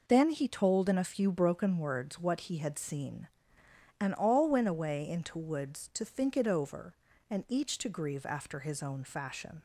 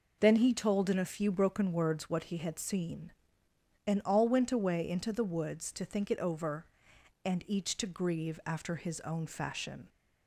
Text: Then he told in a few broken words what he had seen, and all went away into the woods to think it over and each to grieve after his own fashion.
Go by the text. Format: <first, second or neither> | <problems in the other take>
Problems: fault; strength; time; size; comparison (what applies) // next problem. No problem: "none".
second | skips "the"; at 5.3 s